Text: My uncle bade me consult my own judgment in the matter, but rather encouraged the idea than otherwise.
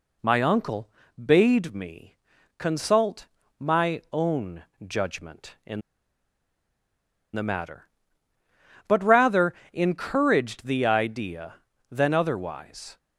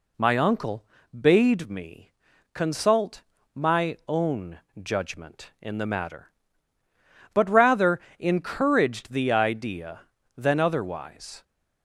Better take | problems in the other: second | pauses between "uncle" and "bade"; slight; at 0.9 s; 0.32 s long; slight in the second // pauses between "me" and "consult"; at 2.1 s; 0.40 s long; also in the second // pauses between "consult" and "my"; slight; at 3.2 s; 0.32 s long; slight in the second // pauses between "own" and "judgment"; slight; at 4.6 s; 0.22 s long; slight in the second // pauses between "in" and "the"; strong; at 5.8 s; 1.5 s long // pauses between "rather" and "encouraged"; slight; at 9.5 s; 0.18 s long; slight in the second

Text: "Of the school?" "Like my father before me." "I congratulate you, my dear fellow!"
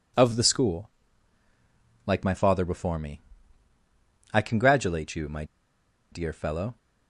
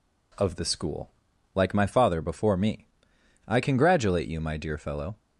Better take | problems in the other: second | pauses between "my" and "dear"; noticeable; at 5.4 s; 0.67 s long

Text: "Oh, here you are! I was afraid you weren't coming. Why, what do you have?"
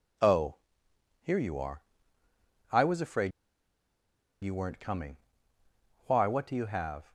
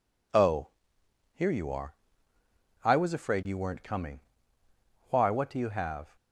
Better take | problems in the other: second | pauses between "afraid" and "you"; at 3.3 s; 1.1 s long

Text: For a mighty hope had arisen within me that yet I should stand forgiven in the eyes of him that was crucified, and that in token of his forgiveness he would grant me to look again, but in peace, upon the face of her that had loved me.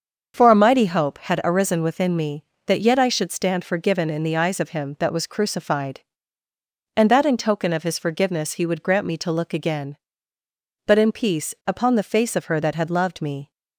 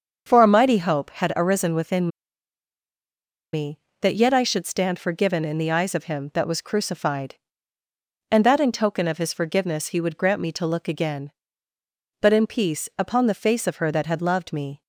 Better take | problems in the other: first | starts louder than the rest; until 1.2 s; 6.5 dB; also in the first // pauses between "within" and "me"; strong; at 2.0 s; 1.4 s long

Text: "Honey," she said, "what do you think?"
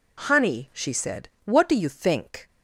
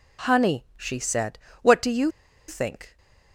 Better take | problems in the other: first | pauses between "you" and "think"; at 2.1 s; 0.37 s long

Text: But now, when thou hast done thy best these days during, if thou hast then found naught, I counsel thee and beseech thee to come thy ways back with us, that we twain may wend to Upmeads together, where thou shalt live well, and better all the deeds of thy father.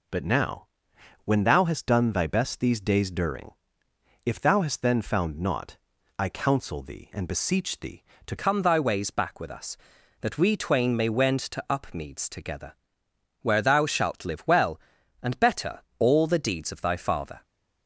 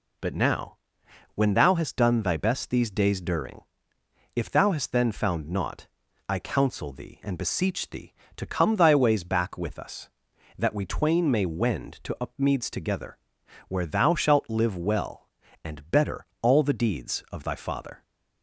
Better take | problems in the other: second | changes voice at "come"; from 8.3 s on; 9.1 s long // pauses between "better" and "all"; slight; at 15.8 s; 0.18 s long; slight in the second

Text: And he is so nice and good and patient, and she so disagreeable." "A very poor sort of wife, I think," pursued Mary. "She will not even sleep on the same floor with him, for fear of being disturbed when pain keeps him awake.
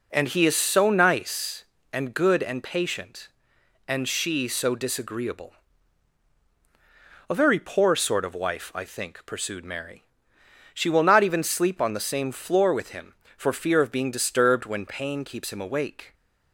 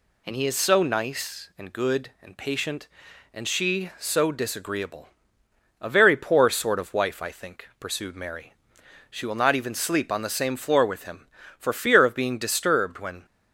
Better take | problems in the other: first | stops before "pain keeps him awake"; at 13.2 s

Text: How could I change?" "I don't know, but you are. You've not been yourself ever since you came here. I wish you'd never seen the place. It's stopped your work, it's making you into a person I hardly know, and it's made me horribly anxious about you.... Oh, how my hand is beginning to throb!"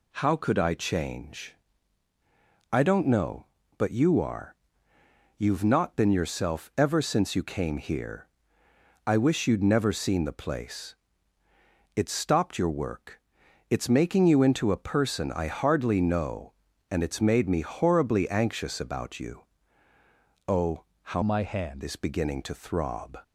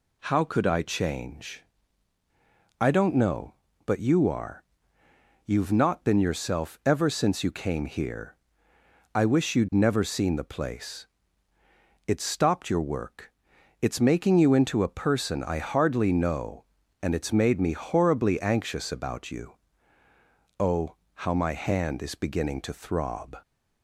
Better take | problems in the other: second | changes voice from "my" to "hand"; from 21.2 to 21.8 s; 0.6 s long

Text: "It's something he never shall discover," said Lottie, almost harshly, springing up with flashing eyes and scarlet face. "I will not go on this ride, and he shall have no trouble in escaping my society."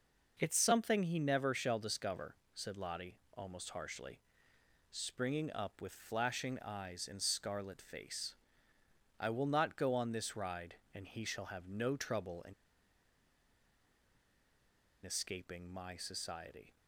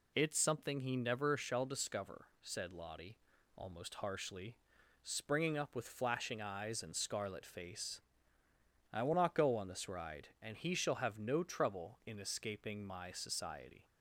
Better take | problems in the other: second | pauses between "in" and "escaping"; strong; at 12.5 s; 2.5 s long

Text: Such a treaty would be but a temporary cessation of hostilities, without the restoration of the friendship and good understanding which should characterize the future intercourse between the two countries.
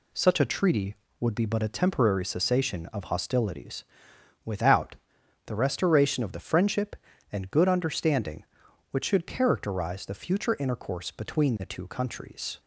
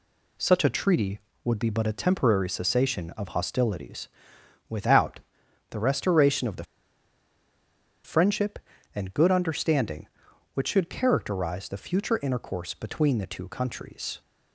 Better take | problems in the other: first | pauses between "without" and "the"; noticeable; at 5.1 s; 0.52 s long; noticeable in the first // pauses between "the" and "friendship"; strong; at 6.6 s; 1.4 s long

